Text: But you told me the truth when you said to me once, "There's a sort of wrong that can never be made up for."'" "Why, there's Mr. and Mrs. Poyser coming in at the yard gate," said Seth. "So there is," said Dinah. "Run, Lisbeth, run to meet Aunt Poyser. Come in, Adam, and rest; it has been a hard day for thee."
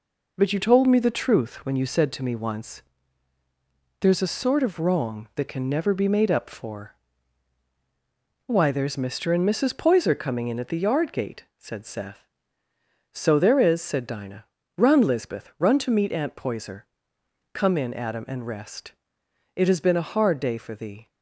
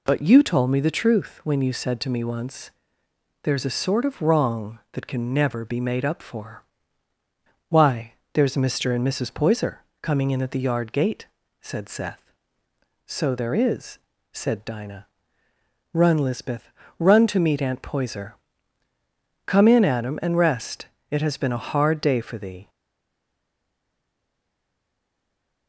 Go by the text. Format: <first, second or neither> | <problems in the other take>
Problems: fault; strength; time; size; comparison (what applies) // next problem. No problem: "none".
first | pauses between "Poyser" and "coming"; slight; at 9.7 s; 0.22 s long // stays silent after the last word; strong; from 22.6 s on; 3.0 s long